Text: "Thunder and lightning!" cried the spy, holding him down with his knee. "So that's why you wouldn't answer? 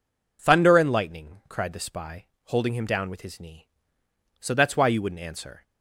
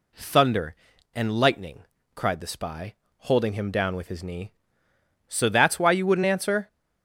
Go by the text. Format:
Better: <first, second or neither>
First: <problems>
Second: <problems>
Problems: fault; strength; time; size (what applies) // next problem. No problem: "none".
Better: neither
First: none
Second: none